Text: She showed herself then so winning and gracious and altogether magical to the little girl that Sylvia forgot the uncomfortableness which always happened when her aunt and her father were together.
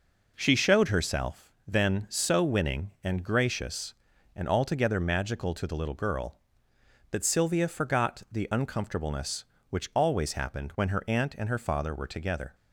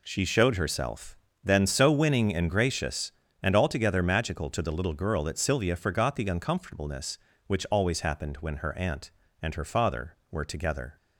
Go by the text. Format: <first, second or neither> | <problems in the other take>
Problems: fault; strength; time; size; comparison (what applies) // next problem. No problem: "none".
neither | pauses between "herself" and "then"; slight; the same in both